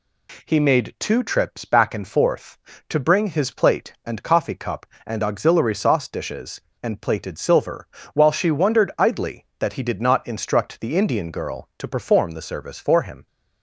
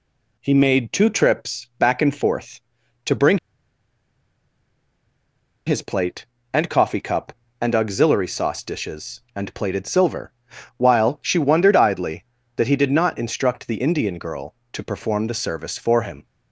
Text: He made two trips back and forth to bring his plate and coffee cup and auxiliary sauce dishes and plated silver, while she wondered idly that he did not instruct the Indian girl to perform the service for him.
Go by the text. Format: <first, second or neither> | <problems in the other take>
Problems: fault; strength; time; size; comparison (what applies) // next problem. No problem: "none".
first | pauses between "bring" and "his"; strong; at 3.3 s; 2.2 s long